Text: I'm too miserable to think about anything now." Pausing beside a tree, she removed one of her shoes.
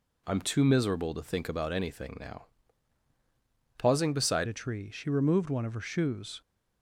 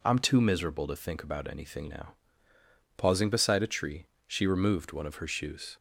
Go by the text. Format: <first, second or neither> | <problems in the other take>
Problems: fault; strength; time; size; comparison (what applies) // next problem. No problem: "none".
second | changes voice at "a"; from 4.4 s on; 2.0 s long